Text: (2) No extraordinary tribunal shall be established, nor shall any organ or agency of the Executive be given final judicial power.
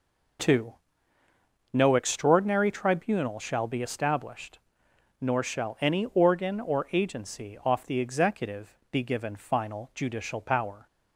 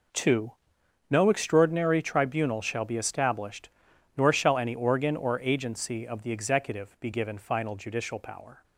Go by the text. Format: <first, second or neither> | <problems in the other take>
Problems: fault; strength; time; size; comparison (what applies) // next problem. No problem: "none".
second | says "off" for "of"; at 7.6 s